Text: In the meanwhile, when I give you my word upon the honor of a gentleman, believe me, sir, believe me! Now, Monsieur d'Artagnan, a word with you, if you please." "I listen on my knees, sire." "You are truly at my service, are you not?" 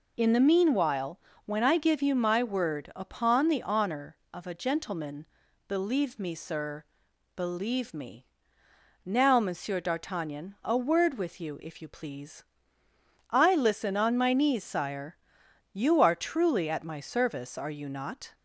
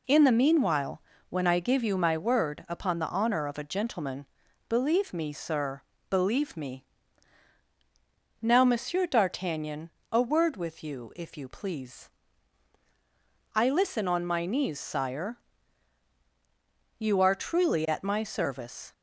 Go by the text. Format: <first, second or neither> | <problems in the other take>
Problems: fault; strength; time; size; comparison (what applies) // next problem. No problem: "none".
first | stops before "are you not"; at 18.9 s